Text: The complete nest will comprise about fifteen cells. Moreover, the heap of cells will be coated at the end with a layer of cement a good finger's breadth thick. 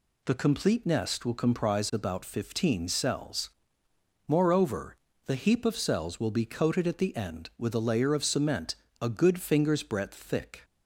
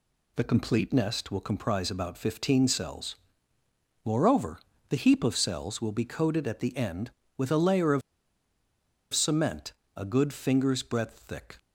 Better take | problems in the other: first | pauses between "of" and "cement"; at 8.0 s; 1.1 s long // pauses between "cement" and "a"; slight; at 9.7 s; 0.22 s long; slight in the first

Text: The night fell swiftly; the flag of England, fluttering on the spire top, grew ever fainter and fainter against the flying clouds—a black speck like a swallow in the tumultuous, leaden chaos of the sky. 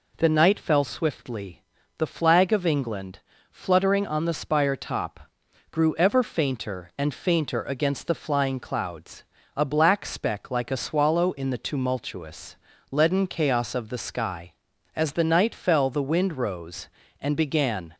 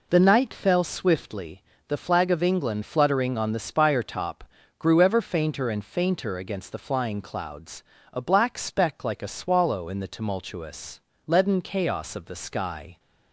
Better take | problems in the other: second | goes on to say "As the night fell the wind rose and began"; strong; from 14.9 s on; 3.0 s long

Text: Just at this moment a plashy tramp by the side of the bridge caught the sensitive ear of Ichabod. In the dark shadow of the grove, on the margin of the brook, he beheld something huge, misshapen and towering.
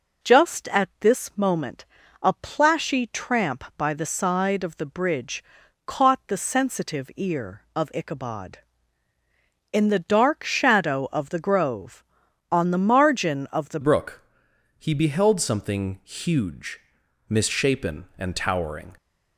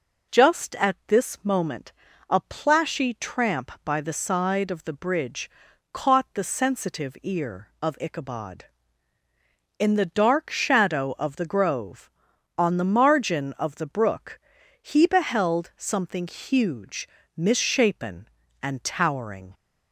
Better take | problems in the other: second | pauses between "moment" and "a"; slight; at 1.8 s; 0.36 s long; slight in the second // pauses between "bridge" and "caught"; at 5.4 s; 0.44 s long; also in the second // changes voice at "brook"; from 13.8 s on; 5.1 s long

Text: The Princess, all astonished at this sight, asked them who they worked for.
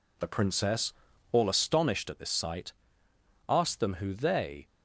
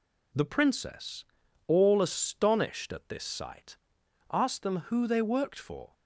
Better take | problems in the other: second | stops before "worked for"; at 4.6 s

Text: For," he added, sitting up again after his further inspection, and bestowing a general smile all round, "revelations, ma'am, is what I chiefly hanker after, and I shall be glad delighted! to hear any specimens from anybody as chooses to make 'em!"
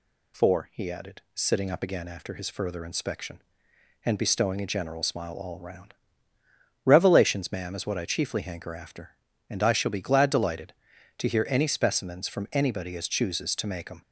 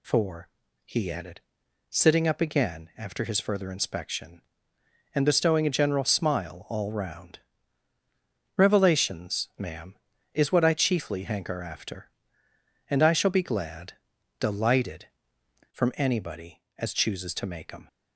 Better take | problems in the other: first | pauses between "glad" and "delighted"; at 13.9 s; 0.44 s long // skips "to hear any specimens"; at 15.4 s

